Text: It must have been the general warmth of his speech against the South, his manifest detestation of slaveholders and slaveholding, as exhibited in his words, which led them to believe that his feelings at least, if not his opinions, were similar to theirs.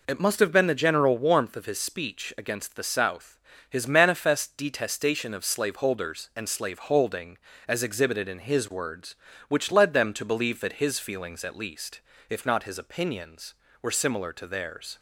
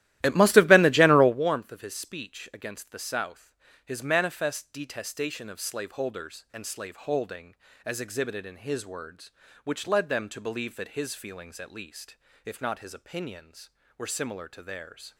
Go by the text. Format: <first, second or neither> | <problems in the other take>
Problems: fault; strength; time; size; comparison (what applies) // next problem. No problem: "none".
first | starts louder than the rest; strong; until 1.5 s; 14.5 dB